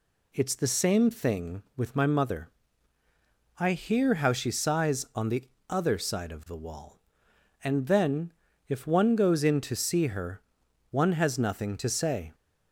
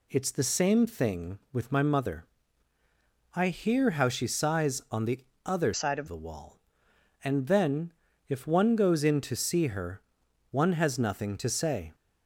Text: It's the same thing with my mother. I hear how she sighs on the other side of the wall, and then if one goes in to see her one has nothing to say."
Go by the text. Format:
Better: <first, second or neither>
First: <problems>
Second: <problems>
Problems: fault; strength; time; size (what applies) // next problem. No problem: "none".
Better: first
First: pauses between "the" and "other"; slight; at 5.4 s; 0.26 s long // pauses between "then" and "if"; slight; at 8.3 s; 0.34 s long // pauses between "her" and "one"; noticeable; at 10.4 s; 0.50 s long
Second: pauses between "the" and "other"; slight; at 5.1 s; 0.26 s long // changes voice from "side" to "of"; from 5.7 to 6.0 s; 0.3 s long // pauses between "then" and "if"; slight; at 7.9 s; 0.34 s long // pauses between "her" and "one"; noticeable; at 10.0 s; 0.50 s long